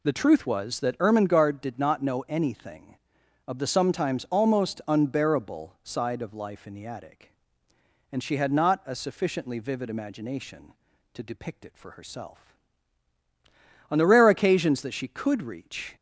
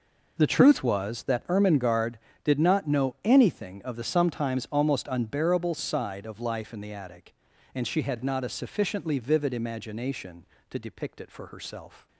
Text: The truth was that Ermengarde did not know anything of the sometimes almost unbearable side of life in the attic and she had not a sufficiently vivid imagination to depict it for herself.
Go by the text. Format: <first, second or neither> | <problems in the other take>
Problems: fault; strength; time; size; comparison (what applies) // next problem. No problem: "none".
second | goes on to say "On the rare occasions that she could reach"; strong; from 13.9 s on; 2.0 s long